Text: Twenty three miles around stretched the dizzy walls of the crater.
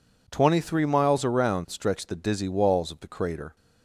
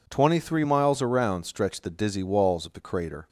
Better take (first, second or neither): neither